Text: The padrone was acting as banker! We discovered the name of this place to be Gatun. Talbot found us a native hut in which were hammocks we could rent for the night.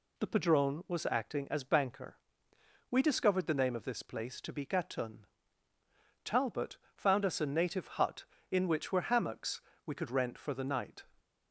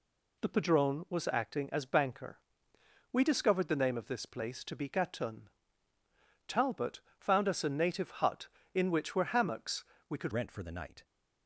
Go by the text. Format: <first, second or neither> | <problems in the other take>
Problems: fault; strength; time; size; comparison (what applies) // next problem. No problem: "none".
first | pauses between "Talbot" and "found"; slight; at 6.9 s; 0.18 s long; slight in the first // pauses between "hammocks" and "we"; slight; at 9.8 s; 0.24 s long; slight in the first // changes voice at "rent"; from 10.3 s on; 0.7 s long